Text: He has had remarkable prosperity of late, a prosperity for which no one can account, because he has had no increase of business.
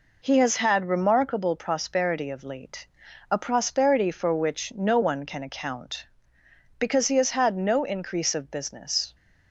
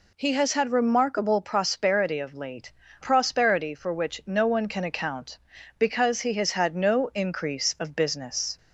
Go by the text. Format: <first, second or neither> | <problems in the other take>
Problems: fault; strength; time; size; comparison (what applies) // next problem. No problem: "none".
first | skips "a"; at 2.8 s